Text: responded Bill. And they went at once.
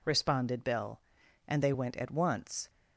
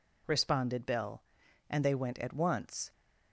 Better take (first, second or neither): neither